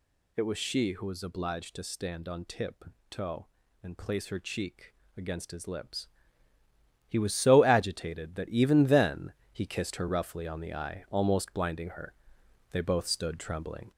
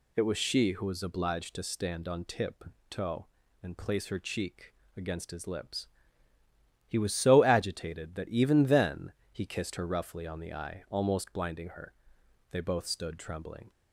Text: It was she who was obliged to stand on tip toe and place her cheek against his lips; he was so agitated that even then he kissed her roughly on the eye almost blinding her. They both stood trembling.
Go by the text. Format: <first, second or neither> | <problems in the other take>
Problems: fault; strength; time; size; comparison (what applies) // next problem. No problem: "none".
second | gets louder; slight; throughout; 3.5 dB // pauses between "tip" and "toe"; slight; at 2.8 s; 0.26 s long; slight in the second // pauses between "cheek" and "against"; slight; at 4.9 s; 0.22 s long; slight in the second // pauses between "then" and "he"; slight; at 9.3 s; 0.20 s long; slight in the second